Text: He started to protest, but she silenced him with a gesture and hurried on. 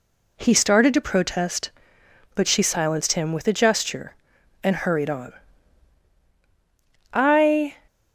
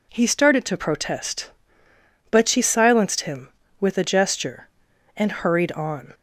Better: second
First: goes on to say "I"; noticeable; from 7.1 s on; 0.64 s long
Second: none

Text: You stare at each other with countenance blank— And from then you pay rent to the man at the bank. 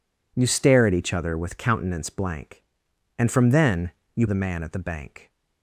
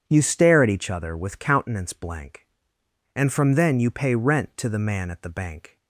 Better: second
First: pauses between "then" and "you"; slight; at 3.9 s; 0.24 s long // skips "pay rent to"; at 4.2 s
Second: none

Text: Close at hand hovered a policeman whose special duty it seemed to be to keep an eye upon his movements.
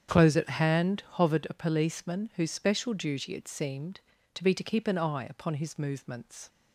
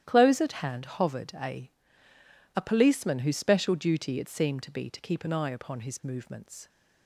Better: first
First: starts louder than the rest; strong; until 1.1 s; 8 dB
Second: starts louder than the rest; strong; until 1.0 s; 11.5 dB // says "a" twice; at 2.5 s

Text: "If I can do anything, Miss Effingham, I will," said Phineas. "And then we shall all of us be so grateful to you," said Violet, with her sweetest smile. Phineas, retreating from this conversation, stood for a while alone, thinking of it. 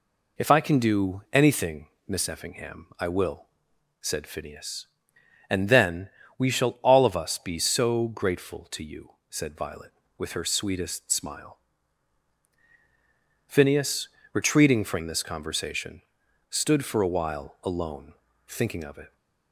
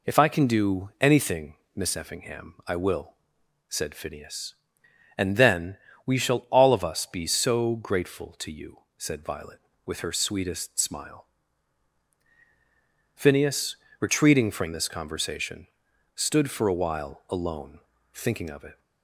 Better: neither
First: pauses between "then" and "we"; slight; at 6.1 s; 0.28 s long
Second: pauses between "then" and "we"; slight; at 5.7 s; 0.28 s long

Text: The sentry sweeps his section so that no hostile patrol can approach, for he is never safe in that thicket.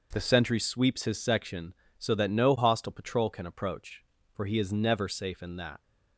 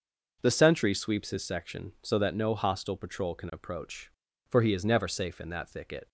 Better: second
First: stops before "thicket"; at 5.8 s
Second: none

